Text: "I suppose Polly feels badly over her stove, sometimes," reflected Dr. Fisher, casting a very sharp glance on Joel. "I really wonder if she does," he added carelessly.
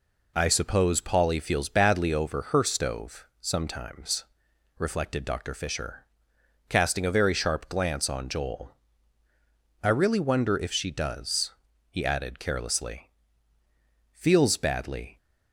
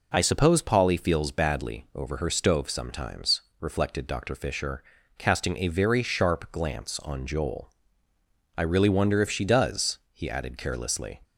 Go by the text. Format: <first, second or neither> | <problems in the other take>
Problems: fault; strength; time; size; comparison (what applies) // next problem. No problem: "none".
second | goes on to say "Feels badly"; noticeable; from 14.1 s on; 1.0 s long